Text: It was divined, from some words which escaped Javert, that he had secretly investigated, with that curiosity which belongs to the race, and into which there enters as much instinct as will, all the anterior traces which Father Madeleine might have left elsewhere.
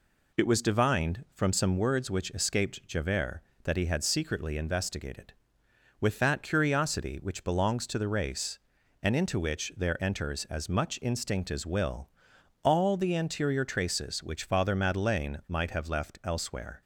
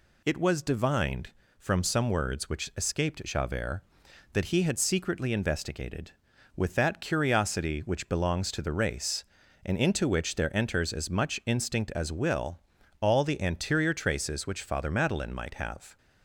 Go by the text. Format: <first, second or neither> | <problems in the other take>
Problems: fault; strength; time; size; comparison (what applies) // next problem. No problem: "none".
first | stops before "left elsewhere"; at 15.9 s